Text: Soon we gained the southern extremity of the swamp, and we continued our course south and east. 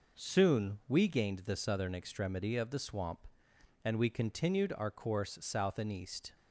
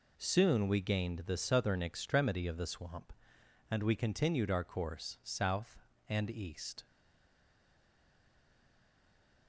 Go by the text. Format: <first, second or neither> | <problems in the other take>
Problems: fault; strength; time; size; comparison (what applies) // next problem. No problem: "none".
first | stays silent after the last word; strong; from 6.8 s on; 2.6 s long